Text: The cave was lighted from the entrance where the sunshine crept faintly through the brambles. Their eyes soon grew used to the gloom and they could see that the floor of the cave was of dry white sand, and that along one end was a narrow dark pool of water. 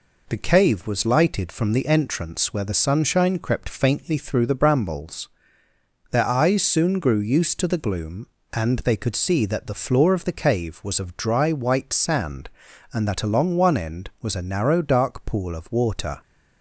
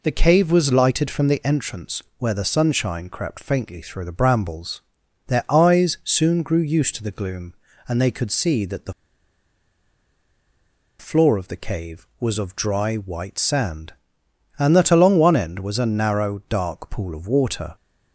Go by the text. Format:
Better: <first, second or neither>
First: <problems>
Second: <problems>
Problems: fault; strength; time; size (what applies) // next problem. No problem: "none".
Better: first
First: none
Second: pauses between "entrance" and "where"; slight; at 2.0 s; 0.16 s long // pauses between "the" and "floor"; strong; at 8.9 s; 2.0 s long